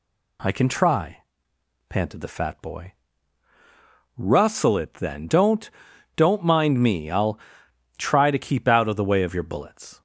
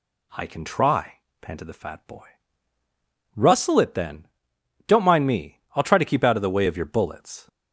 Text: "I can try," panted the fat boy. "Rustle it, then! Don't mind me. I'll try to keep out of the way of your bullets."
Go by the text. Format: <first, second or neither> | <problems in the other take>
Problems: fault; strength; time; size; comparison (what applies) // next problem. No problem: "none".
second | says "Don't" twice; at 6.1 s // pauses between "I'll" and "try"; noticeable; at 7.3 s; 0.60 s long